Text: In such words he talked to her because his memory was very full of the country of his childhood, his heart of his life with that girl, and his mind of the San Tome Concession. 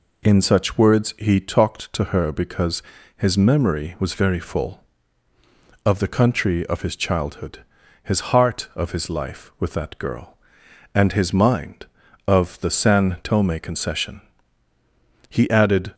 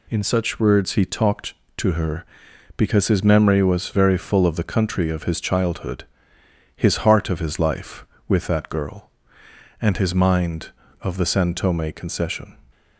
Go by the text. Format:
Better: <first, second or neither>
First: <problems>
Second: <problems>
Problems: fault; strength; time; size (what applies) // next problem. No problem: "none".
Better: second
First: pauses between "because" and "his"; slight; at 2.8 s; 0.34 s long // goes on to say "He added"; noticeable; from 15.2 s on; 0.66 s long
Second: none